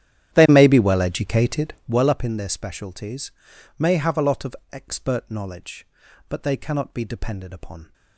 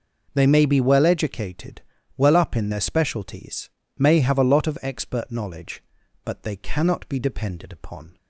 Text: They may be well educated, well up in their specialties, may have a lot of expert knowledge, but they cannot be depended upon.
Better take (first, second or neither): second